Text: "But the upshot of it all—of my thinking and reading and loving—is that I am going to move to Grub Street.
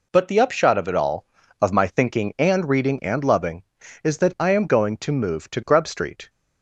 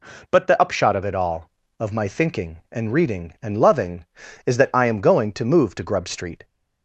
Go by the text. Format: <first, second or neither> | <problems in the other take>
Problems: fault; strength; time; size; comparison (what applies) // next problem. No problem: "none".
neither | none